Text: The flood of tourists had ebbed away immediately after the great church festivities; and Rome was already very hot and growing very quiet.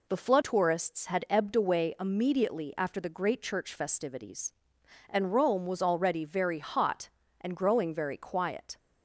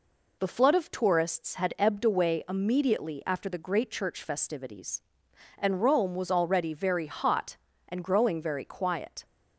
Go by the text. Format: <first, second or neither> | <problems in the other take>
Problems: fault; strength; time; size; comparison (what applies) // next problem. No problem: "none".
second | skips "of"; at 0.4 s